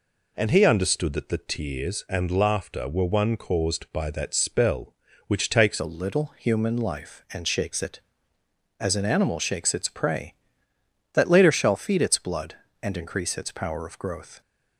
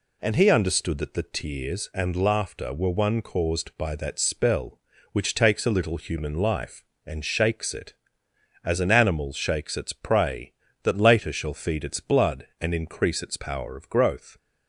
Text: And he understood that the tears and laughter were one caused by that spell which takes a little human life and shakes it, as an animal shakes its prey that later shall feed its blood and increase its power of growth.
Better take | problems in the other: second | changes voice at "a"; from 5.7 s on; 8.7 s long

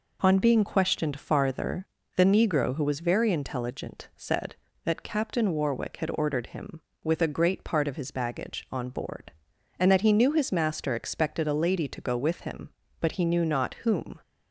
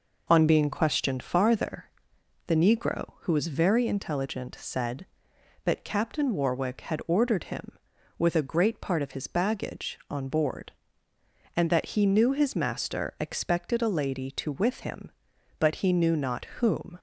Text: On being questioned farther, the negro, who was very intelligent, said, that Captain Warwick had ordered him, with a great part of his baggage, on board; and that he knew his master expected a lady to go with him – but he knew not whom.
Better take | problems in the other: first | skips "go"; at 14.5 s

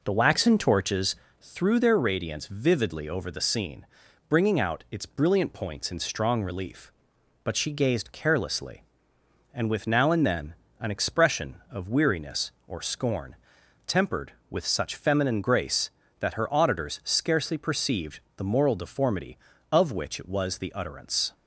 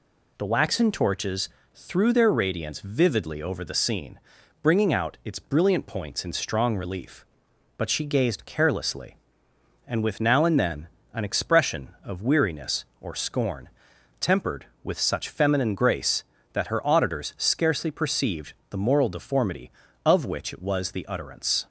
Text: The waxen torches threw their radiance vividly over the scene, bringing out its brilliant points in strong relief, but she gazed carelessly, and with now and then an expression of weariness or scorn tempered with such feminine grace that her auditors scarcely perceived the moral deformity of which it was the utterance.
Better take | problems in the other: second | starts louder than the rest; noticeable; until 1.5 s; 4.5 dB // pauses between "torches" and "threw"; slight; at 1.1 s; 0.26 s long; slight in the second // pauses between "then" and "an"; slight; at 10.5 s; 0.24 s long; slight in the second // pauses between "scorn" and "tempered"; noticeable; at 13.3 s; 0.50 s long; noticeable in the second // pauses between "perceived" and "the"; slight; at 18.1 s; 0.18 s long; slight in the second

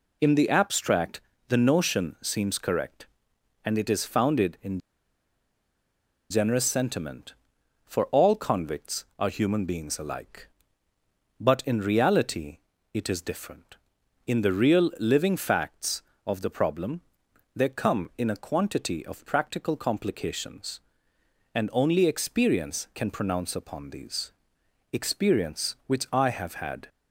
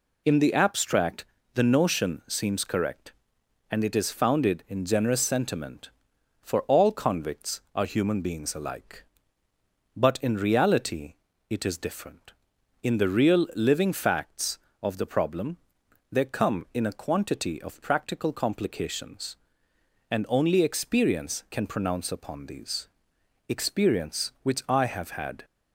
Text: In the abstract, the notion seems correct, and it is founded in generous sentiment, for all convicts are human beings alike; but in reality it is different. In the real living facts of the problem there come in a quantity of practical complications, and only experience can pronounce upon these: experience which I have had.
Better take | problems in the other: second | pauses between "in" and "generous"; strong; at 4.7 s; 1.5 s long // pauses between "reality" and "it"; slight; at 12.5 s; 0.34 s long; slight in the second // pauses between "problem" and "there"; noticeable; at 17.0 s; 0.54 s long; noticeable in the second

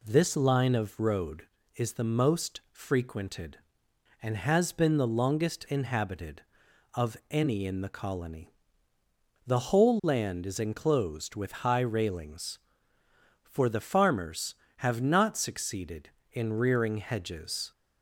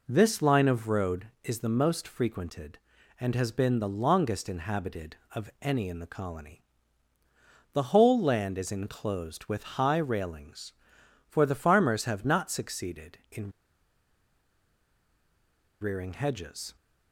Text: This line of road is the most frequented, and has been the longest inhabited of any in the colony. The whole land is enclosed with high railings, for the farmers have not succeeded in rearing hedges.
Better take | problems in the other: first | pauses between "in" and "rearing"; strong; at 13.4 s; 2.3 s long

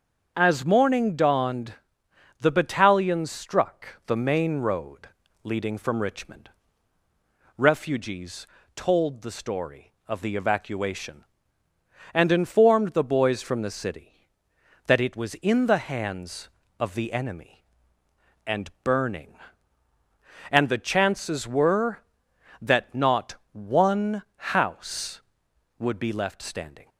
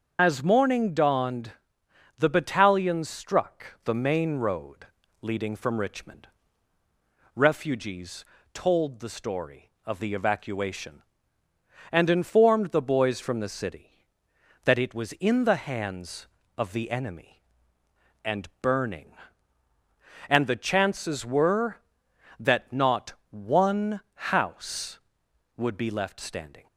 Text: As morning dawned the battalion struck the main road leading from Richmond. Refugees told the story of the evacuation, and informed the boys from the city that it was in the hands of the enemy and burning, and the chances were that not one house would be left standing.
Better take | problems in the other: first | loses the start of "As"; at 0.1 s; 45 ms // starts louder than the rest; until 1.2 s; 7 dB; also in the first // pauses between "dawned" and "the"; noticeable; at 1.5 s; 0.66 s long; noticeable in the first // pauses between "road" and "leading"; at 4.8 s; 0.38 s long; also in the first // pauses between "Refugees" and "told"; slight; at 8.2 s; 0.30 s long; slight in the first // pauses between "not" and "one"; slight; at 23.1 s; 0.16 s long; slight in the first

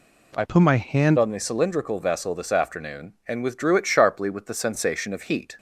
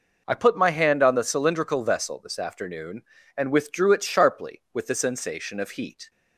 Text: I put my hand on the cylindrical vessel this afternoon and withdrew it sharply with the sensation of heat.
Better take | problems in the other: second | changes voice from "put" to "hand"; from 0.4 to 1.1 s; 0.7 s long

